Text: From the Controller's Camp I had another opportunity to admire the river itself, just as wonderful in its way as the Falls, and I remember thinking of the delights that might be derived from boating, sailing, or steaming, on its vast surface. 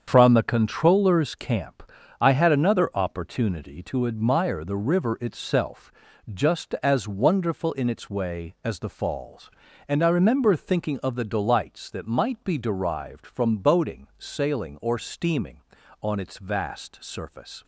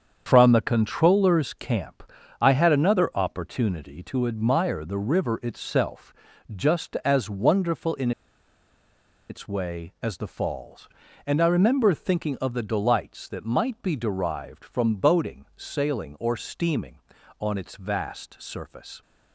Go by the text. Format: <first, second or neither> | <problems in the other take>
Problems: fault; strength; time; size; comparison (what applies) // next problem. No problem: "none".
first | starts louder than the rest; strong; until 1.2 s; 7.5 dB; strong in the first // pauses between "Camp" and "I"; at 2.0 s; 0.38 s long; also in the first // pauses between "in" and "its"; at 8.1 s; 1.1 s long